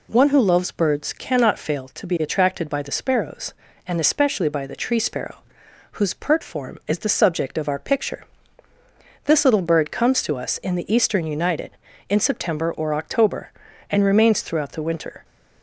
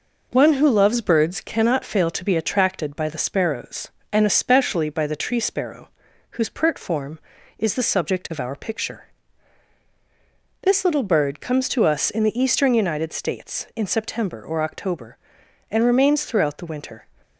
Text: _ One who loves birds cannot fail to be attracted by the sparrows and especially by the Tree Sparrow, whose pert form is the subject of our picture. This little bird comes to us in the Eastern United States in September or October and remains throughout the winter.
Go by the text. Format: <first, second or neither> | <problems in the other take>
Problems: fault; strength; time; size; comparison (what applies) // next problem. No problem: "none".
second | skips "States"; at 11.8 s